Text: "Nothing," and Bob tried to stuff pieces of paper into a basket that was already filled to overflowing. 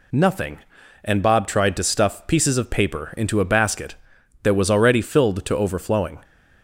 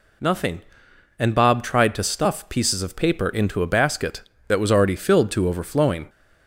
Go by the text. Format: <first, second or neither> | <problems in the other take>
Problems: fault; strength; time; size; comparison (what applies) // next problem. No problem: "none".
neither | none